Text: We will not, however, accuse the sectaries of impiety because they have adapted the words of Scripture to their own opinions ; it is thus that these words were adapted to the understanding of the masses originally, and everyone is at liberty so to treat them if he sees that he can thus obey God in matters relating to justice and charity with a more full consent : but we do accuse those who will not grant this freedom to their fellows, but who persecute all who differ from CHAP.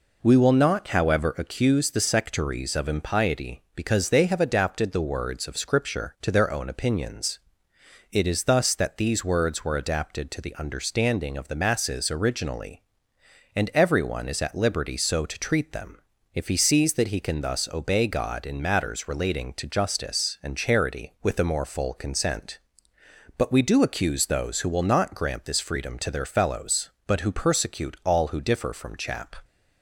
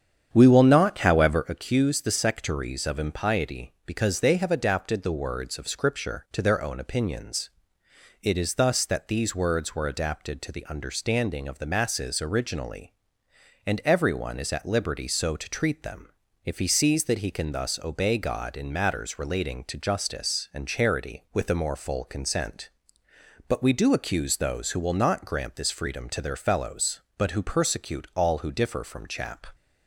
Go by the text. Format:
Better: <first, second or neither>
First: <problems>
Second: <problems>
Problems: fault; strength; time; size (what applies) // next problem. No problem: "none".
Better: first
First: pauses between "them" and "if"; at 15.9 s; 0.38 s long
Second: starts louder than the rest; strong; until 1.5 s; 8.5 dB // pauses between "them" and "if"; at 16.0 s; 0.38 s long